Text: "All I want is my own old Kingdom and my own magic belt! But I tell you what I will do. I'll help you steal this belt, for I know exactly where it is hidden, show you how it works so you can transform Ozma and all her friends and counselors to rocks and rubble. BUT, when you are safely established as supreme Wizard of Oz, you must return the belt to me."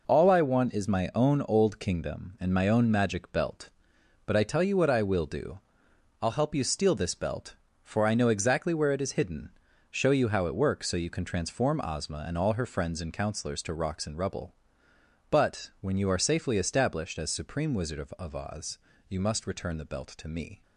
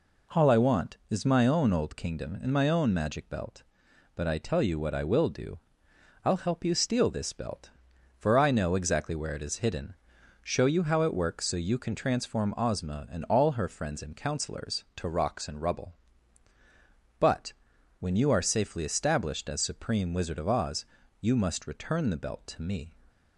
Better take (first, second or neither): second